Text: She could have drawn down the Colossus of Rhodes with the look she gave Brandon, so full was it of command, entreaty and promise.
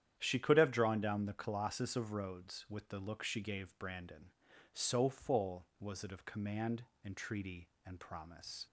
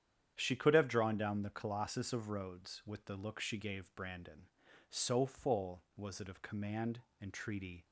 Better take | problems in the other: first | starts louder than the rest; strong; until 1.3 s; 9 dB; strong in the first // stops before "and promise"; at 7.8 s

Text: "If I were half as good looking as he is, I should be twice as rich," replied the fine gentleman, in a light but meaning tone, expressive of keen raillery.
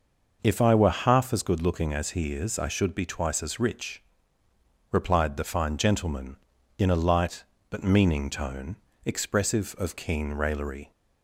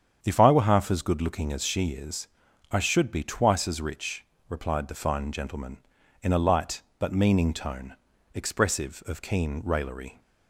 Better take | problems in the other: first | starts louder than the rest; strong; until 1.2 s; 8 dB // says "she" for "he"; at 1.6 s

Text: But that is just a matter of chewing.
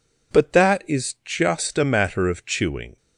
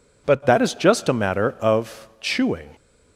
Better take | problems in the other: first | changes voice at "that"; from 0.4 s on; 2.3 s long

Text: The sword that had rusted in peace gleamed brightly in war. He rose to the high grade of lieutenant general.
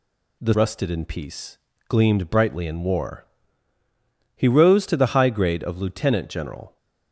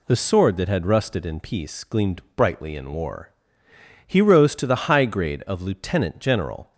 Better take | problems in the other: second | skips "sword that had"; at 0.5 s // pauses between "peace" and "gleamed"; slight; at 1.5 s; 0.30 s long

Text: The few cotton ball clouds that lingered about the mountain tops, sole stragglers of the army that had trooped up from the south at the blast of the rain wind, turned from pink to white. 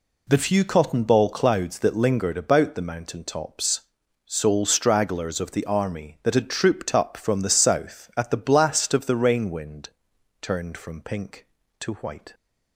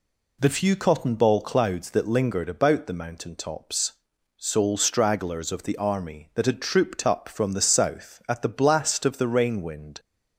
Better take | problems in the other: first | stops before "turned from pink to white"; at 9.9 s

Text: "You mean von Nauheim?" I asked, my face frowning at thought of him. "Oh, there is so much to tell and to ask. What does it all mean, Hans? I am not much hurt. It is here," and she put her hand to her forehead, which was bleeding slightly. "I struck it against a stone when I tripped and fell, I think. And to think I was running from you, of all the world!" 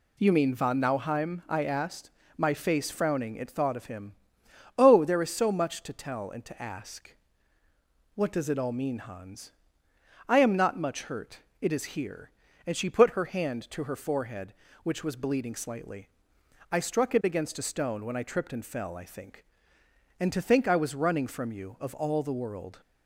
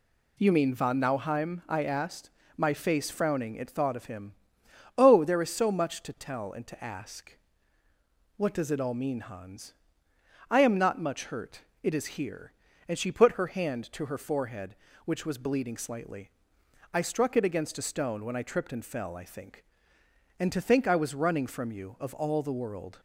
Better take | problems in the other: neither | none

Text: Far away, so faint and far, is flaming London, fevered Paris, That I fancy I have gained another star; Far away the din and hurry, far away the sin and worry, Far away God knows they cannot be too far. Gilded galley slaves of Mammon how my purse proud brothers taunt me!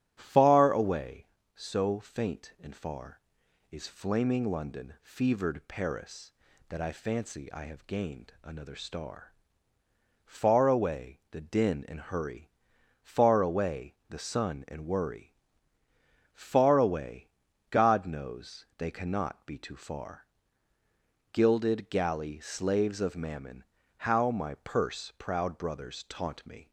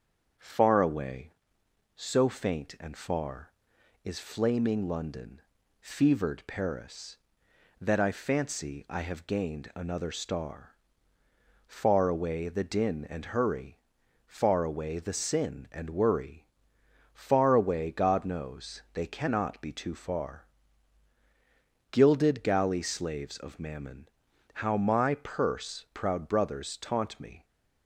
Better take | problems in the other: second | starts louder than the rest; strong; until 1.1 s; 10.5 dB; also in the second // says "sun" for "sin"; at 14.1 s // pauses between "away" and "God"; at 17.2 s; 0.42 s long // pauses between "Mammon" and "how"; slight; at 23.6 s; 0.36 s long; noticeable in the second

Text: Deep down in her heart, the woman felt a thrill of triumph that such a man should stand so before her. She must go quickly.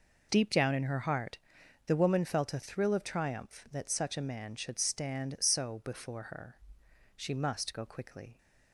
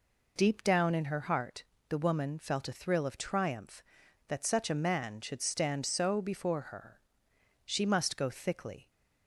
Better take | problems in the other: first | says "thickly" for "quickly"; at 8.2 s

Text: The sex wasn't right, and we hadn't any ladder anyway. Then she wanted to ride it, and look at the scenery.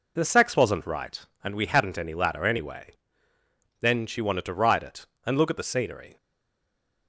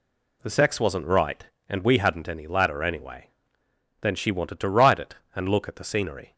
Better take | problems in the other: second | stays silent after the last word; slight; from 6.1 s on; 0.9 s long

